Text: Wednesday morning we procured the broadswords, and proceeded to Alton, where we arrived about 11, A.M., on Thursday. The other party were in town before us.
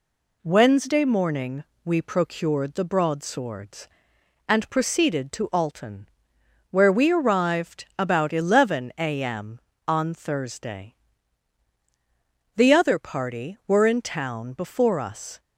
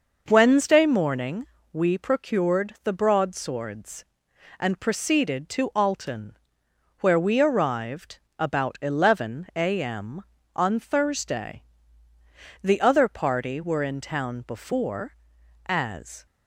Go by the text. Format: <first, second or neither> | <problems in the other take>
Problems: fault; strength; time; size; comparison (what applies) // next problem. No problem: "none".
first | pauses between "morning" and "we"; slight; at 1.4 s; 0.26 s long; slight in the first // pauses between "arrived" and "about"; slight; at 8.1 s; 0.18 s long // says "as" for "us"; at 15.6 s